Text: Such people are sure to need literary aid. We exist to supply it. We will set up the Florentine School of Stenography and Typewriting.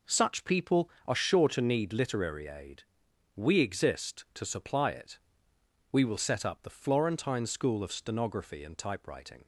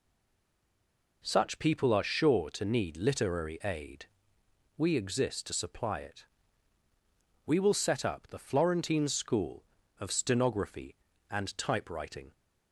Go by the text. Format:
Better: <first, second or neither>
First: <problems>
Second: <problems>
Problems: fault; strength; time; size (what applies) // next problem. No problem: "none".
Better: first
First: none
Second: stays silent before the first word; noticeable; until 1.2 s; 1.2 s long